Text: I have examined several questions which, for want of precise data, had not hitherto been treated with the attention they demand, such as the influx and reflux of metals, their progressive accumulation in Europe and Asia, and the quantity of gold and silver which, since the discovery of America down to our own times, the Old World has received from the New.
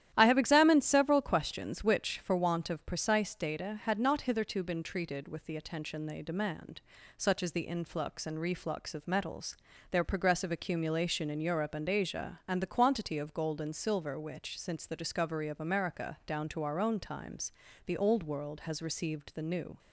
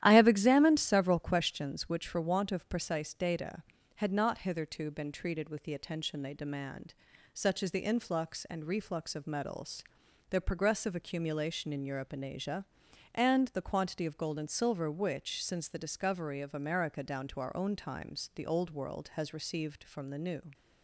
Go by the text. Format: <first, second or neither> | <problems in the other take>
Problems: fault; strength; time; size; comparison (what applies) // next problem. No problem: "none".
second | starts louder than the rest; strong; until 1.1 s; 11.5 dB; strong in the second // skips "from"; at 19.3 s